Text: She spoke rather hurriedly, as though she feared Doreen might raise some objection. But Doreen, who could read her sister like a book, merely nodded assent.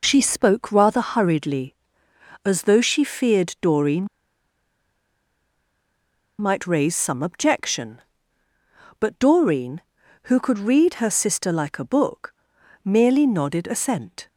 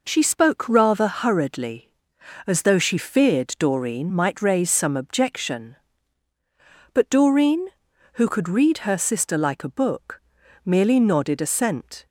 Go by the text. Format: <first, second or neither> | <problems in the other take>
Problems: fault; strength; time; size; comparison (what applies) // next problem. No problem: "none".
second | pauses between "Doreen" and "might"; strong; at 4.0 s; 2.3 s long